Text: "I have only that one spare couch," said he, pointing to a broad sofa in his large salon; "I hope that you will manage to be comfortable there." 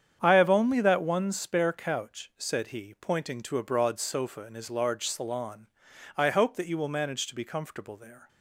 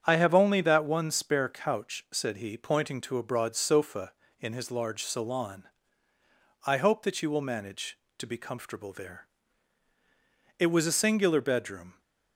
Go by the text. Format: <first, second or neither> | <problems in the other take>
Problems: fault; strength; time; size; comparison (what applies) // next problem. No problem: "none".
first | starts louder than the rest; strong; until 1.0 s; 8 dB; strong in the first // goes on to say "It was a singular bedroom"; from 10.5 s on; 1.4 s long